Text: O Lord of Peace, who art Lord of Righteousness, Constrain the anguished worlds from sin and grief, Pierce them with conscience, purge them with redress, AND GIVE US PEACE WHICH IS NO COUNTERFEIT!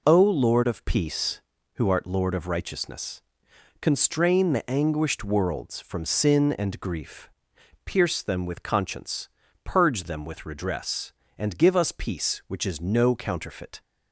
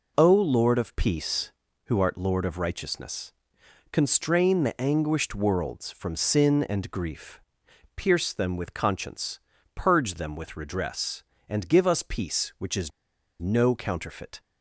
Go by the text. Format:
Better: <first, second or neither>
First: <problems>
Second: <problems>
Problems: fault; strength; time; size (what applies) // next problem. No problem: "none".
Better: first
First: none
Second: pauses between "IS" and "NO"; noticeable; at 12.9 s; 0.50 s long